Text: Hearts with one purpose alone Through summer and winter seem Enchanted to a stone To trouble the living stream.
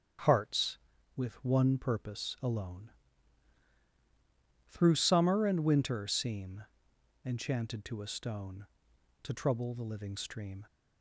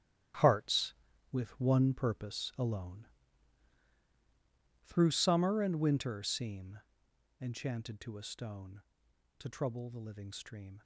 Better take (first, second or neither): first